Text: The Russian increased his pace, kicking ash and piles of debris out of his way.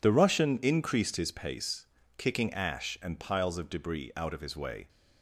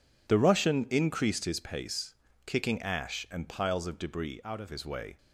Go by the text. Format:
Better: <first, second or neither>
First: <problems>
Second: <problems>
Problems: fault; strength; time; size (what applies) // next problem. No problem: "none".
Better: first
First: none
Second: changes voice from "out" to "of"; from 4.4 to 4.6 s; 0.2 s long